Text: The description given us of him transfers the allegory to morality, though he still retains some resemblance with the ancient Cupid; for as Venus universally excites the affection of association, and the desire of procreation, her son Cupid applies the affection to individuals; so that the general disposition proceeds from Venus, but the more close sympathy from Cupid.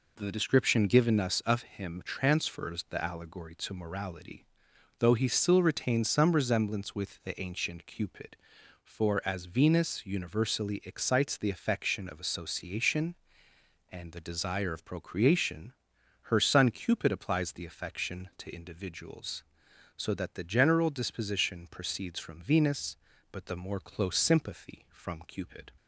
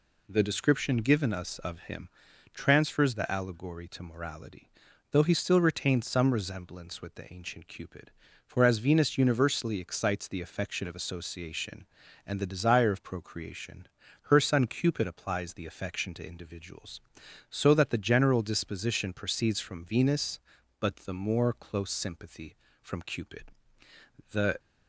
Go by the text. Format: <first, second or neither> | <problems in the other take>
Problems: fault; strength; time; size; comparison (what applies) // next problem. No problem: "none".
first | pauses between "him" and "transfers"; noticeable; at 2.0 s; 0.46 s long // goes on to say "The"; slight; from 24.3 s on; 0.28 s long